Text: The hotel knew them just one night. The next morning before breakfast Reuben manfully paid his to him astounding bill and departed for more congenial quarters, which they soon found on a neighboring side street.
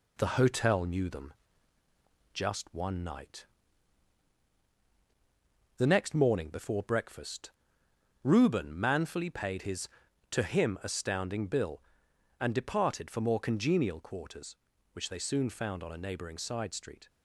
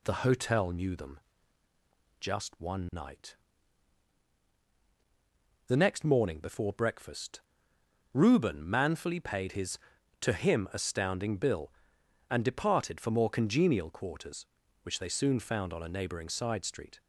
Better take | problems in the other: second | gets quieter; slight; throughout; 3.5 dB // pauses between "them" and "just"; at 1.3 s; 1.0 s long; also in the second // pauses between "breakfast" and "Reuben"; noticeable; at 7.5 s; 0.72 s long; noticeable in the second

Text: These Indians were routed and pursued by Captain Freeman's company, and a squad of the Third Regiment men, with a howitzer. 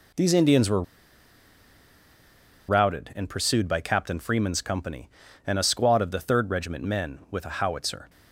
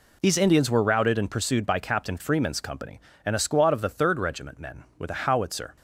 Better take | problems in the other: second | pauses between "were" and "routed"; strong; at 0.8 s; 1.8 s long

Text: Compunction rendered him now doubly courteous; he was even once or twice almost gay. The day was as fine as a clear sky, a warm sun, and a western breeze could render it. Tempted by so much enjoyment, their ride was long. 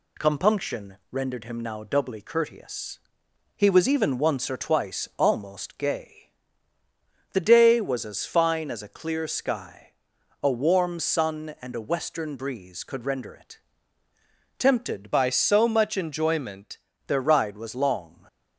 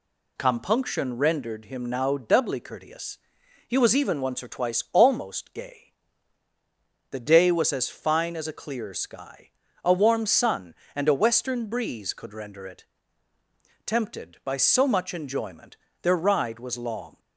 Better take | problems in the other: second | changes voice from "by" to "enjoyment"; from 15.1 to 16.7 s; 1.6 s long // stays silent after the last word; slight; from 18.0 s on; 0.5 s long

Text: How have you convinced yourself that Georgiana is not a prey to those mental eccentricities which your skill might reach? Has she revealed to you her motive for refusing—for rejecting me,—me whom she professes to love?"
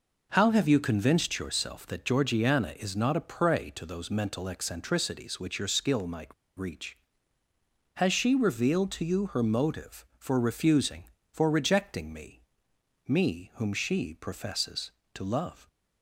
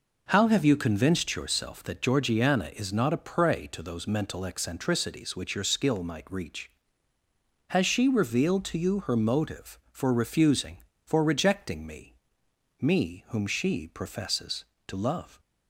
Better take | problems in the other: second | pauses between "might" and "reach"; slight; at 6.3 s; 0.25 s long

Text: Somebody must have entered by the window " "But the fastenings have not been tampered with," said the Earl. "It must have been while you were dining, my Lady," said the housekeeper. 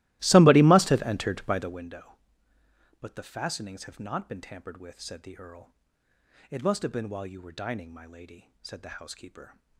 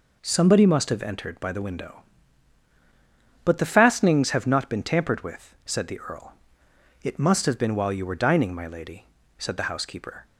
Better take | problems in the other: second | starts louder than the rest; strong; until 1.9 s; 17.5 dB

